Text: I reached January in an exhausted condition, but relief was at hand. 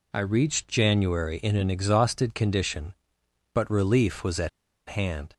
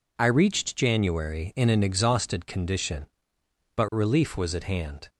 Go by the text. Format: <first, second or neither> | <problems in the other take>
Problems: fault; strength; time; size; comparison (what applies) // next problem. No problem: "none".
second | pauses between "at" and "hand"; at 4.4 s; 0.39 s long